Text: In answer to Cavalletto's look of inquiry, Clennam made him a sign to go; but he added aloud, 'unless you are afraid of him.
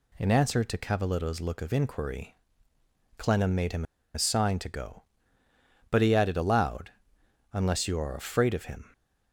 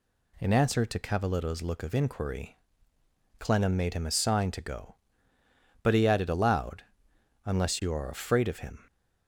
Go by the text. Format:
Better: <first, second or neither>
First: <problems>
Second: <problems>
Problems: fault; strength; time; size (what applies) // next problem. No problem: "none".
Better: second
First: pauses between "him" and "a"; slight; at 3.8 s; 0.31 s long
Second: none